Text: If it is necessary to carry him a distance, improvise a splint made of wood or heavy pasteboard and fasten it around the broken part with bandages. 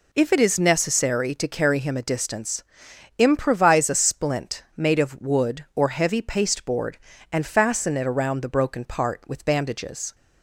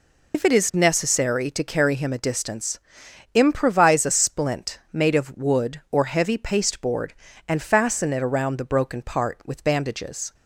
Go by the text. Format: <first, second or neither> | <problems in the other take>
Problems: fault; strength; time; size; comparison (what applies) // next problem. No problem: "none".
first | loses the start of "If"; at 0.3 s; 85 ms